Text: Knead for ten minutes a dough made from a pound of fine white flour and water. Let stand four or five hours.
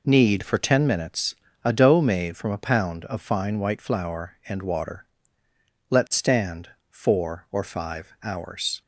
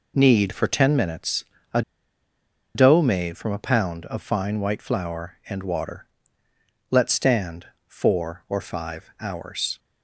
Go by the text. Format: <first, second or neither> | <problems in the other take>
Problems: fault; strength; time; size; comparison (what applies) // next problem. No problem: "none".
first | pauses between "minutes" and "a"; slight; at 1.4 s; 0.30 s long; slight in the first // pauses between "a" and "dough"; noticeable; at 1.8 s; 0.93 s long // pauses between "stand" and "four"; slight; at 7.6 s; 0.20 s long; slight in the first